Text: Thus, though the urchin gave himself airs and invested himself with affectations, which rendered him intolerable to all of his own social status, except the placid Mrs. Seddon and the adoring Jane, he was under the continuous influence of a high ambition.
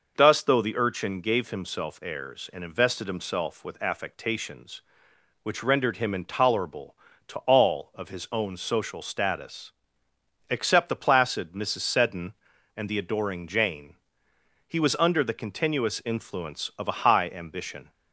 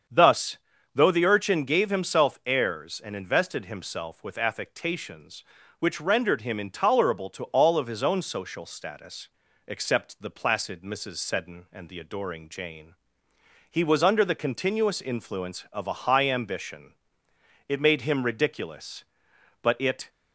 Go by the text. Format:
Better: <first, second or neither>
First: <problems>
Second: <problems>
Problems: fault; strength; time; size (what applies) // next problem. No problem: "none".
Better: first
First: none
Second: starts louder than the rest; strong; until 1.4 s; 7 dB // goes on to say "It made him ridiculous but it"; strong; from 17.6 s on; 2.4 s long